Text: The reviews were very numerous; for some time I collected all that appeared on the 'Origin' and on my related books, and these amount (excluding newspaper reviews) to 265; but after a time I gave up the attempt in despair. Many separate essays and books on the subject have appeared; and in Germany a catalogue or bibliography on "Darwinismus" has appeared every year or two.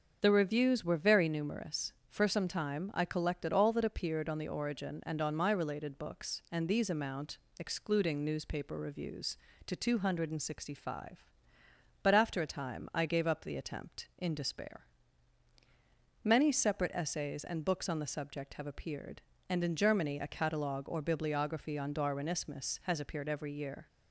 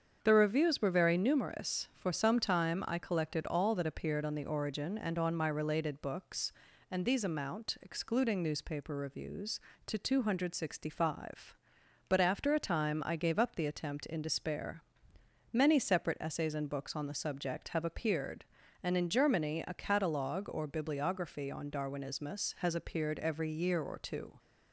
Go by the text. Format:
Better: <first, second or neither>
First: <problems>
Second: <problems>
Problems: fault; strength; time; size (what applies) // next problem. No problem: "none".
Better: second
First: starts louder than the rest; until 1.2 s; 6.5 dB // stops before "or two"; at 23.8 s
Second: starts louder than the rest; strong; until 1.2 s; 7.5 dB